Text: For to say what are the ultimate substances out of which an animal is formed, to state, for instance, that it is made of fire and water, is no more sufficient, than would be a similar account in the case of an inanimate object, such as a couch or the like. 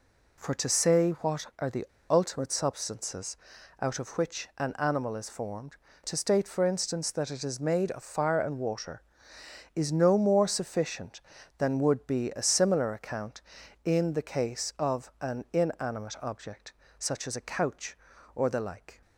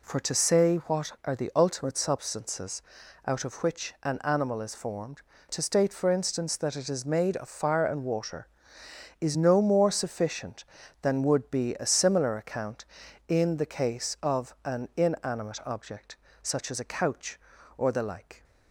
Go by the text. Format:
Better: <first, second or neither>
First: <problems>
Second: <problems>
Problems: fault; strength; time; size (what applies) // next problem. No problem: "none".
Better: second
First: pauses between "the" and "ultimate"; slight; at 1.8 s; 0.26 s long // pauses between "substances" and "out"; at 3.3 s; 0.44 s long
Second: pauses between "substances" and "out"; at 2.8 s; 0.44 s long